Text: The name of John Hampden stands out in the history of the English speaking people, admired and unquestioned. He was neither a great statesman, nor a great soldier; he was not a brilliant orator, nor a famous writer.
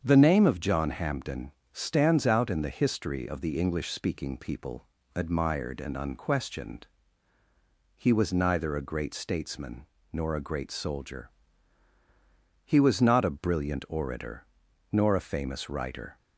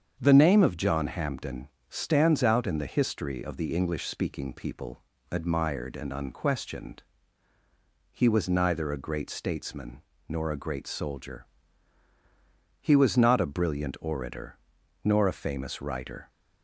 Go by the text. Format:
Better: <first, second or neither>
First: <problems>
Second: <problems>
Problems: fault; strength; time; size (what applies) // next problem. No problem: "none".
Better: neither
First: starts louder than the rest; strong; until 1.0 s; 7.5 dB // pauses between "Hampden" and "stands"; slight; at 1.5 s; 0.22 s long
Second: starts louder than the rest; strong; until 1.2 s; 7.5 dB // pauses between "Hampden" and "stands"; slight; at 1.6 s; 0.22 s long